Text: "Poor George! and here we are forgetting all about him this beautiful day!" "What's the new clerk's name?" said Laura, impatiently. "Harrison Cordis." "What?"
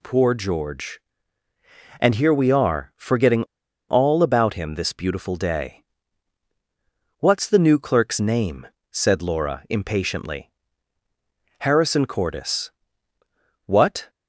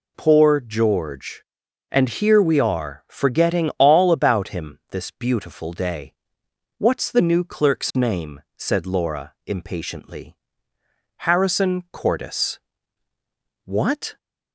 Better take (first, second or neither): second